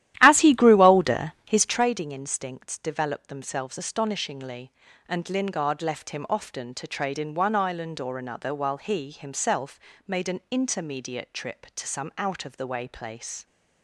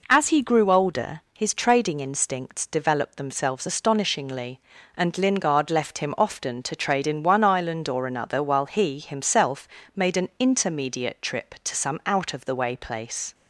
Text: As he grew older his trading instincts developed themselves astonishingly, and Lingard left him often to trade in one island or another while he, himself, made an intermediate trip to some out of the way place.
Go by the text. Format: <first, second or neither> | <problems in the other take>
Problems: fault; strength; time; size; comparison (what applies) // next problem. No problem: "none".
second | starts louder than the rest; strong; until 1.8 s; 13 dB